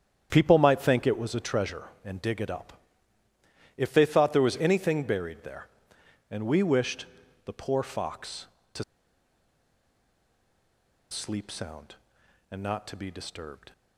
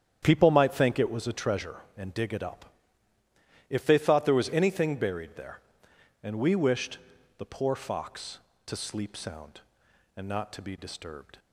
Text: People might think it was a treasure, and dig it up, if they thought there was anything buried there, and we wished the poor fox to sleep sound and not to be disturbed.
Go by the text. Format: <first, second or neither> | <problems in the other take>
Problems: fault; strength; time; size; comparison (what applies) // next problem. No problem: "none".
second | starts louder than the rest; strong; until 1.3 s; 9 dB; strong in the second // pauses between "wished" and "the"; at 7.0 s; 0.38 s long; also in the second // pauses between "to" and "sleep"; strong; at 8.8 s; 2.2 s long